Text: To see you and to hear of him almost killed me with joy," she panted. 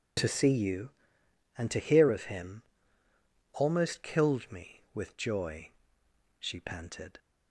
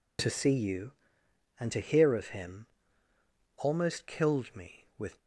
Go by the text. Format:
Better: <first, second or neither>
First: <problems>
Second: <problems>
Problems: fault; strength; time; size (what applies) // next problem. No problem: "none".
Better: first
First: pauses between "him" and "almost"; noticeable; at 2.6 s; 0.92 s long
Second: pauses between "him" and "almost"; noticeable; at 2.6 s; 0.92 s long // stops before "joy she panted"; at 5.2 s